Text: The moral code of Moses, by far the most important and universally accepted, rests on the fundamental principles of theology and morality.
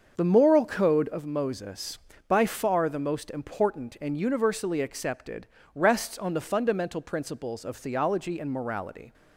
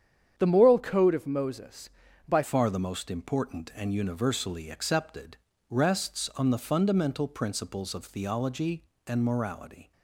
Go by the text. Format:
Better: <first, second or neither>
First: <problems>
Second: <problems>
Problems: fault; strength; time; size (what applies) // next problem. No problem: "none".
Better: first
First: starts louder than the rest; until 1.1 s; 6.5 dB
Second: starts louder than the rest; strong; until 1.3 s; 8.5 dB // changes voice at "far"; from 2.4 s on; 7.5 s long